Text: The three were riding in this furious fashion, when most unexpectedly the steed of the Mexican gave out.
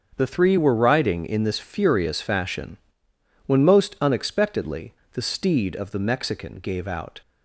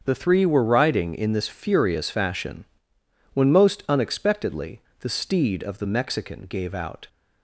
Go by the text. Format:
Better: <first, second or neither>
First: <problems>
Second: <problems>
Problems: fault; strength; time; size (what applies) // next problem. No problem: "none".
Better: neither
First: starts louder than the rest; until 1.1 s; 7 dB // pauses between "unexpectedly" and "the"; slight; at 4.9 s; 0.20 s long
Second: starts louder than the rest; until 1.0 s; 7 dB // pauses between "unexpectedly" and "the"; slight; at 4.8 s; 0.20 s long